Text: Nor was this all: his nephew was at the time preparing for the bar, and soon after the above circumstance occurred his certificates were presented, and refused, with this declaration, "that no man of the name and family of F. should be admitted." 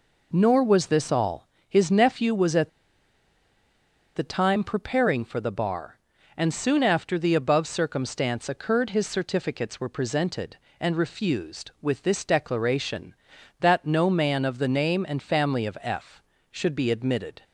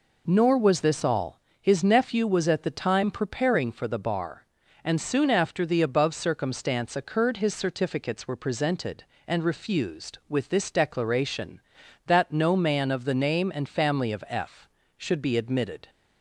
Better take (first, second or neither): second